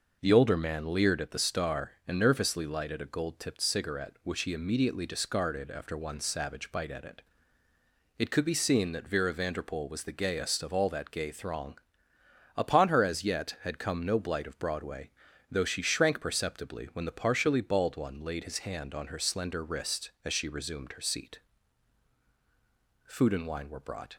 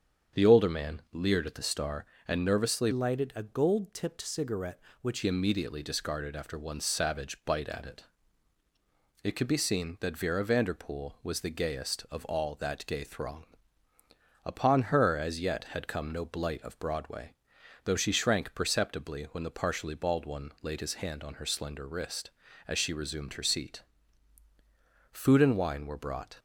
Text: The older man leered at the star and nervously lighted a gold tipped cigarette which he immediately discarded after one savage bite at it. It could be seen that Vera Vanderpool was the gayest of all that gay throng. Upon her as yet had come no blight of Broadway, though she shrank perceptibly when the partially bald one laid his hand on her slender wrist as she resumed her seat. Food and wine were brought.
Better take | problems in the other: first | starts louder than the rest; strong; until 1.4 s; 7.5 dB // changes voice from "lighted" to "which"; from 2.9 to 5.2 s; 2.3 s long

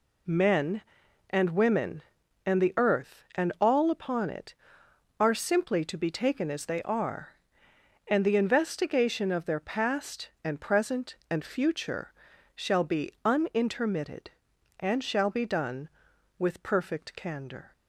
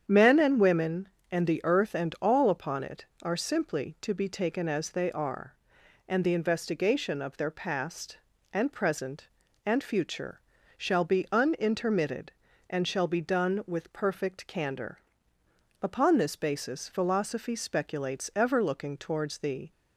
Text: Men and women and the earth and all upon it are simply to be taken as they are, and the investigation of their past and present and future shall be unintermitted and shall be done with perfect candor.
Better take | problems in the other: first | starts louder than the rest; strong; until 1.0 s; 8 dB // pauses between "future" and "shall"; slight; at 10.4 s; 0.36 s long; also in the first // goes on to say "Upon this basis philosophy speculates ever looking towards the"; strong; from 15.8 s on; 3.8 s long

